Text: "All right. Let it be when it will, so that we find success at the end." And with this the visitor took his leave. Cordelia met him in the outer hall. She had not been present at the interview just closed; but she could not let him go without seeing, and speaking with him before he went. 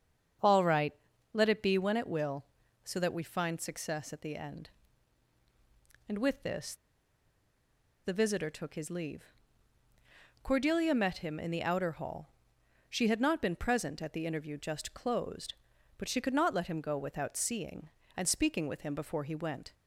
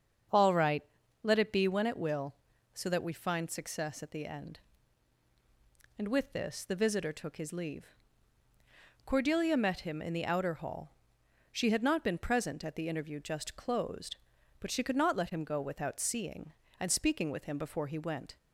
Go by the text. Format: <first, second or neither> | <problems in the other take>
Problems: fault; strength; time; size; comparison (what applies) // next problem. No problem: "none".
second | starts louder than the rest; strong; until 1.8 s; 7 dB; strong in the second // pauses between "this" and "the"; strong; at 6.7 s; 1.3 s long